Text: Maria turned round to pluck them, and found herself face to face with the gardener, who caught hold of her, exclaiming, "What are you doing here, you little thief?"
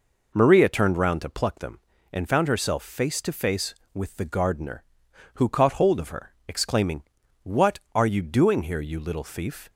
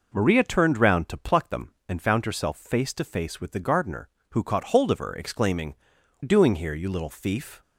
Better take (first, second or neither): first